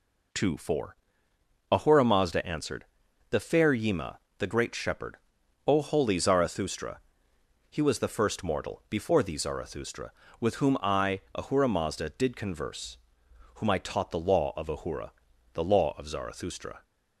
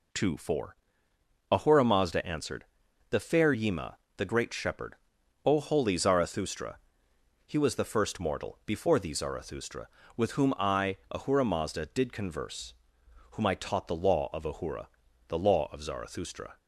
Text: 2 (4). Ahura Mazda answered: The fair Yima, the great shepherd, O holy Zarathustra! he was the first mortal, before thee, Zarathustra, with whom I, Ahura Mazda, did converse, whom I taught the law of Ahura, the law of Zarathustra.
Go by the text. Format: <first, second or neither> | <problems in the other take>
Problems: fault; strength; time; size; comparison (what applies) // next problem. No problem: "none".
neither | none